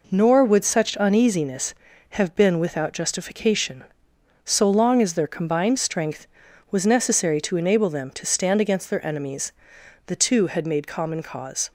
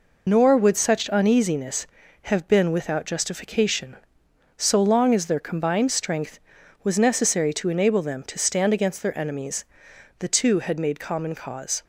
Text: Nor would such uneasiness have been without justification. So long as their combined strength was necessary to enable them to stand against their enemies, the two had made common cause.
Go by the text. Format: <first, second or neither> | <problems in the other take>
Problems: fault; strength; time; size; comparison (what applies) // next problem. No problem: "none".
first | loses the start of "Nor"; at 0.2 s; 80 ms